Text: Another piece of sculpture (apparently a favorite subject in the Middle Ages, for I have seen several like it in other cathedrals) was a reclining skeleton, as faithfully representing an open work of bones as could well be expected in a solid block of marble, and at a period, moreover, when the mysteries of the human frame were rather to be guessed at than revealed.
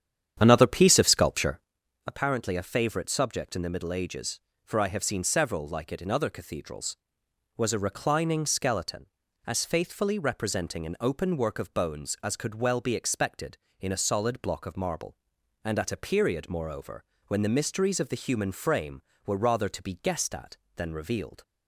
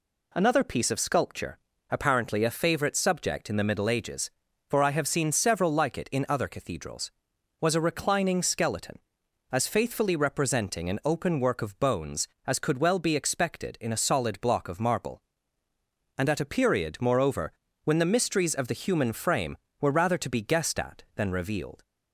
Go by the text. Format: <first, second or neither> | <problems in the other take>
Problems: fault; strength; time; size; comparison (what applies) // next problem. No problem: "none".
second | starts louder than the rest; strong; until 1.8 s; 9 dB